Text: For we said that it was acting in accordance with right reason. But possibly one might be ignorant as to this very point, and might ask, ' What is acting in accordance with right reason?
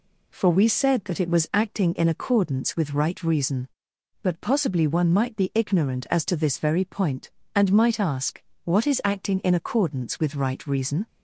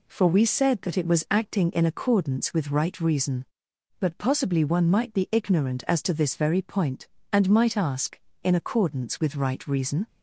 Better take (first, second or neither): first